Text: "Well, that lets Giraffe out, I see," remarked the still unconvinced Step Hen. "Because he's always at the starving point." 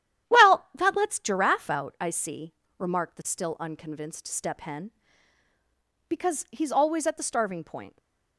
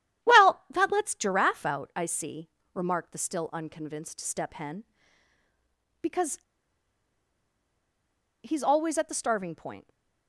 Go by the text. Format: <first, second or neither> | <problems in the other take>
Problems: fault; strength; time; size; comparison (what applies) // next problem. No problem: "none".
first | starts louder than the rest; strong; until 1.3 s; 11 dB; strong in the first // pauses between "Because" and "he's"; strong; at 6.3 s; 2.0 s long